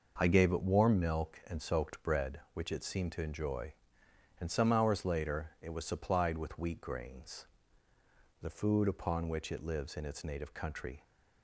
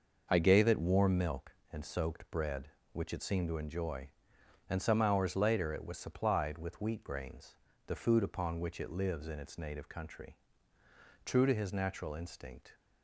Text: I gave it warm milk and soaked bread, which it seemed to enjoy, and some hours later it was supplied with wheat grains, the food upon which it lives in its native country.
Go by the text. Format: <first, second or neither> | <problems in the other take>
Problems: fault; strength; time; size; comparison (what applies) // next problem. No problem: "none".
first | goes on to say "True to his natural instinct"; from 11.2 s on; 1.5 s long